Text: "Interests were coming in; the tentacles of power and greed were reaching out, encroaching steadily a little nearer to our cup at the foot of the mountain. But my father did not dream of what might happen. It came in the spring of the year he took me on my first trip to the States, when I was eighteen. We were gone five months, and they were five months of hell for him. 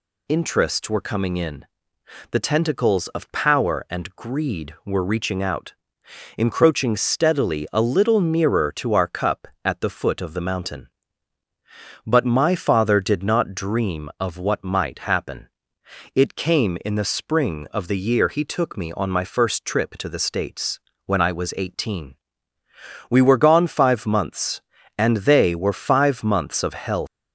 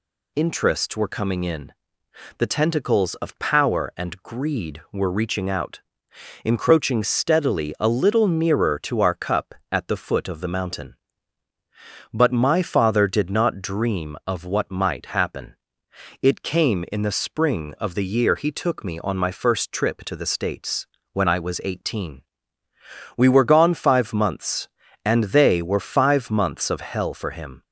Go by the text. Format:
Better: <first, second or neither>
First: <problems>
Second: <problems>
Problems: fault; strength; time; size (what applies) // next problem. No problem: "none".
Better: second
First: stops before "for him"; at 27.0 s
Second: none